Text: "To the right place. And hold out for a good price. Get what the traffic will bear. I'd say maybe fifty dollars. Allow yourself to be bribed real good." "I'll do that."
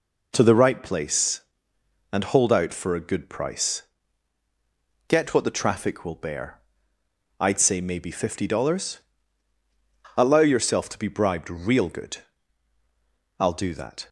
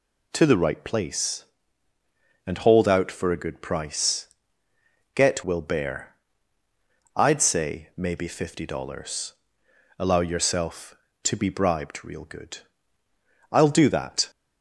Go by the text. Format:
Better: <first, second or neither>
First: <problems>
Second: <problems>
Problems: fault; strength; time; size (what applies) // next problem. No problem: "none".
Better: first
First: none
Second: skips "what the traffic"; at 5.4 s